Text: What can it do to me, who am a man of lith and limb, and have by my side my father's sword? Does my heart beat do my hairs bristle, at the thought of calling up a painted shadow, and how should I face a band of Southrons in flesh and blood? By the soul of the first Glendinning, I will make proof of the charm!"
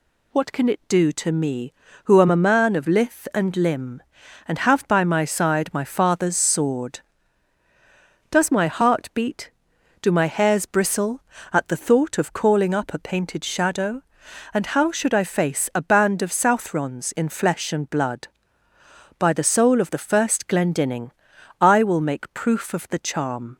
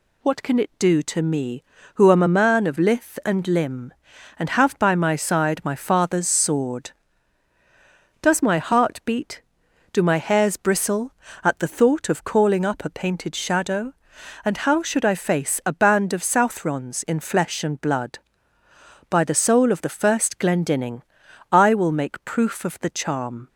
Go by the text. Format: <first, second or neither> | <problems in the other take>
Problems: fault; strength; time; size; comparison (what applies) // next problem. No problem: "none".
neither | none